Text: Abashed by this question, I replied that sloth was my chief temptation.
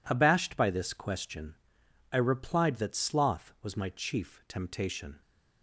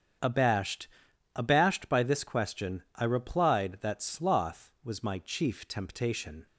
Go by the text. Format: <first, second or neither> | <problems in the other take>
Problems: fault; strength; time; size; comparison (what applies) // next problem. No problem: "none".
first | starts louder than the rest; strong; until 1.6 s; 8 dB // says "Abashed" twice; at 1.3 s